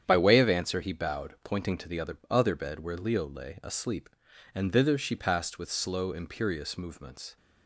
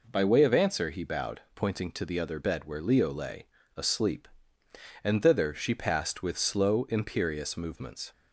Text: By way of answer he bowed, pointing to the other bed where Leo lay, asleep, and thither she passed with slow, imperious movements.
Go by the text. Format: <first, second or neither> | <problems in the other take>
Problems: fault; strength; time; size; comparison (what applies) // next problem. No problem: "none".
second | starts louder than the rest; strong; until 1.0 s; 9 dB // says "other" twice; at 2.2 s